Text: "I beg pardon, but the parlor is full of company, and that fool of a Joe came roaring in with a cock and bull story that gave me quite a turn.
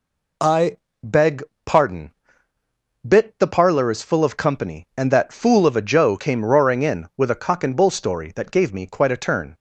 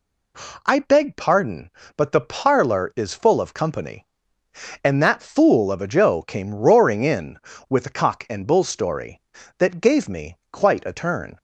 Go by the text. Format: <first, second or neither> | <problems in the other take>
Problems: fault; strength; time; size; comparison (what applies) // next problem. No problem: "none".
second | pauses between "I" and "beg"; slight; at 0.7 s; 0.26 s long // pauses between "beg" and "pardon"; slight; at 1.4 s; 0.22 s long // says "bit" for "but"; at 3.0 s